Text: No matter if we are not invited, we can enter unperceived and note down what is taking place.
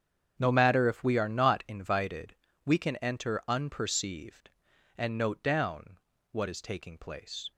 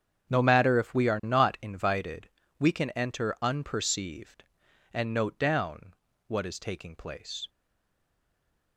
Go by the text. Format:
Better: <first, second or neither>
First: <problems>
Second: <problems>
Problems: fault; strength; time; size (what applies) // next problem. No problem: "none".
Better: first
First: starts louder than the rest; strong; until 1.3 s; 8 dB // pauses between "down" and "what"; slight; at 5.9 s; 0.36 s long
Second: starts louder than the rest; strong; until 1.3 s; 8 dB // pauses between "down" and "what"; slight; at 5.9 s; 0.36 s long // stays silent after the last word; noticeable; from 7.4 s on; 1.3 s long